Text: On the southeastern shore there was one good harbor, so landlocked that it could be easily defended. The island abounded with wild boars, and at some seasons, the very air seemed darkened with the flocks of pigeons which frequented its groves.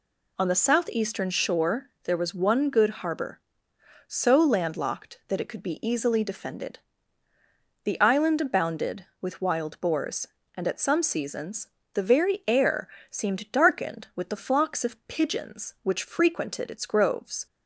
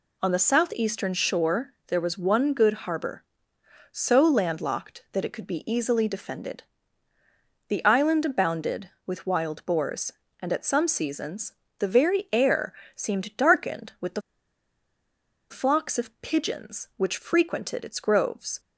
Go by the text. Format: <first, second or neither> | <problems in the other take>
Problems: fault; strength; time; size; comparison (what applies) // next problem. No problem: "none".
first | pauses between "air" and "seemed"; slight; at 12.7 s; 0.22 s long; slight in the first // pauses between "the" and "flocks"; strong; at 14.2 s; 1.2 s long